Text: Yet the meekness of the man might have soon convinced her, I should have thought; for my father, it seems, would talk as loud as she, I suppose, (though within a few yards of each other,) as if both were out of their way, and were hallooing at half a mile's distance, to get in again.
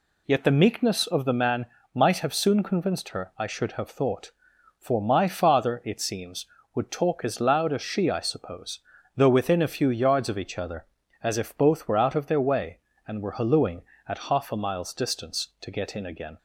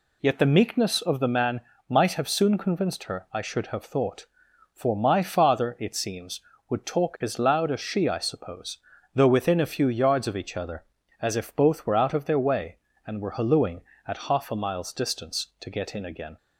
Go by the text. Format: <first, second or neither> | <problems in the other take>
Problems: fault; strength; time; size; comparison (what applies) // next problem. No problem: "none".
neither | pauses between "man" and "might"; slight; the same in both